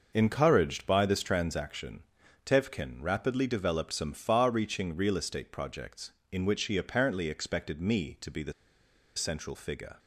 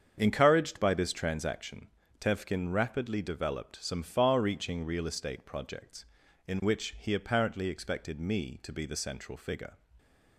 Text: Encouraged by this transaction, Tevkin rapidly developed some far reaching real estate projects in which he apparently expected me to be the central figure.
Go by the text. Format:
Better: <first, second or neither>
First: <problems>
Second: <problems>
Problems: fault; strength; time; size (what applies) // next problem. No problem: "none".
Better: second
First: starts louder than the rest; noticeable; until 1.1 s; 6 dB // pauses between "the" and "central"; noticeable; at 8.5 s; 0.63 s long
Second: starts louder than the rest; strong; until 1.1 s; 7.5 dB